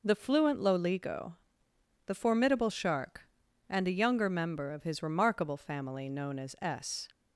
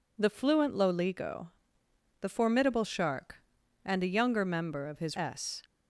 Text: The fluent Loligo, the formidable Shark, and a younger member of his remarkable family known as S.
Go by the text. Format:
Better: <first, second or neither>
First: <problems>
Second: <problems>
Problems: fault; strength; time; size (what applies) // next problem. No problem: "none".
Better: first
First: none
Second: skips "remarkable family known as"; at 5.1 s